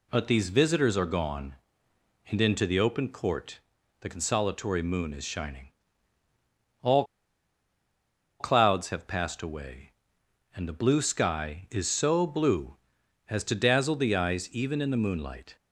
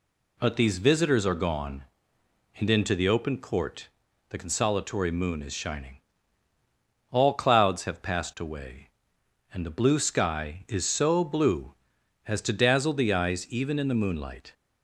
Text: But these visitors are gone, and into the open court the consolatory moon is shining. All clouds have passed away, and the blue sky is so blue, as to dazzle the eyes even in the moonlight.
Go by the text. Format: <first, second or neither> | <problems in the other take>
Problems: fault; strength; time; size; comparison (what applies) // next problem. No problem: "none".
second | pauses between "court" and "the"; at 3.5 s; 0.40 s long; also in the second // pauses between "All" and "clouds"; strong; at 7.0 s; 1.3 s long